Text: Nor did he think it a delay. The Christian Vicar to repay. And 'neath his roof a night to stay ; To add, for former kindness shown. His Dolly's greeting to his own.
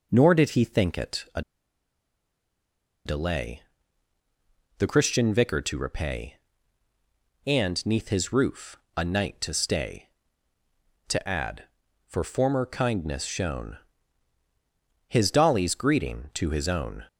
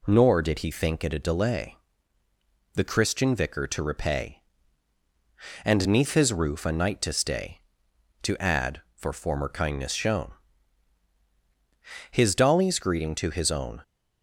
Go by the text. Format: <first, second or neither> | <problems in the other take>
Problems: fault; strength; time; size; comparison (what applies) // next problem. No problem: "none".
second | pauses between "a" and "delay"; strong; at 1.4 s; 1.6 s long // pauses between "roof" and "a"; slight; at 8.7 s; 0.18 s long